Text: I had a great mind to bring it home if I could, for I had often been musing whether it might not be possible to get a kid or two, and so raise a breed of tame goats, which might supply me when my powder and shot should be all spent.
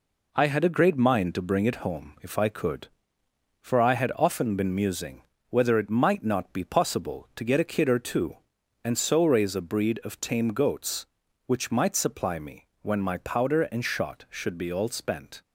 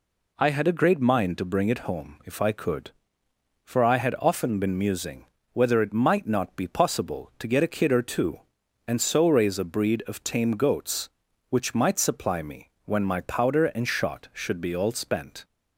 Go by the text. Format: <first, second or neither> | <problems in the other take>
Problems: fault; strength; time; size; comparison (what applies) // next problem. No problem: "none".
second | gets quieter; noticeable; throughout; 5 dB // pauses between "musing" and "whether"; slight; at 5.2 s; 0.26 s long; slight in the second // pauses between "me" and "when"; slight; at 12.6 s; 0.16 s long; slight in the second